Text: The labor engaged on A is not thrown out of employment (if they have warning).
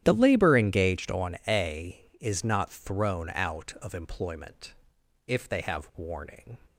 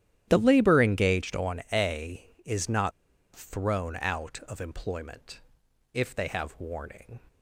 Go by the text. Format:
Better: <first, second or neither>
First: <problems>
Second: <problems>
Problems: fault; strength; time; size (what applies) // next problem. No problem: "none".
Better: first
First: starts louder than the rest; strong; until 1.0 s; 11 dB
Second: starts louder than the rest; strong; until 1.3 s; 11 dB // pauses between "not" and "thrown"; at 2.9 s; 0.43 s long